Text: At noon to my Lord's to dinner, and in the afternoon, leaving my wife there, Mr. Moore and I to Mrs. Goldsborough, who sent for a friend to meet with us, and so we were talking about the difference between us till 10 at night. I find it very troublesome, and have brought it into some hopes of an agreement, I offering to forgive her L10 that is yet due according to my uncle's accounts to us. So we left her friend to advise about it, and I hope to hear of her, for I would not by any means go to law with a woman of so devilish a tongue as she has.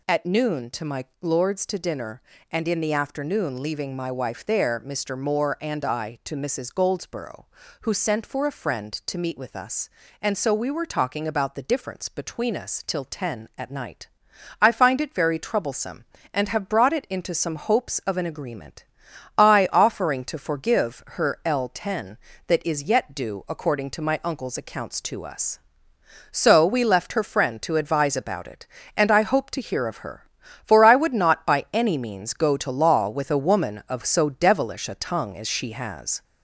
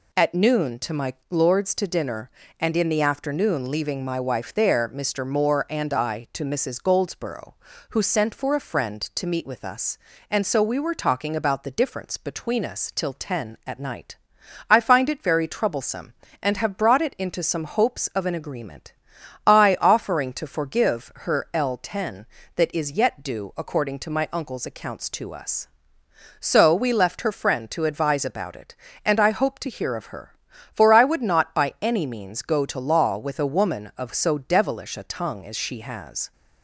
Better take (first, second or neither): second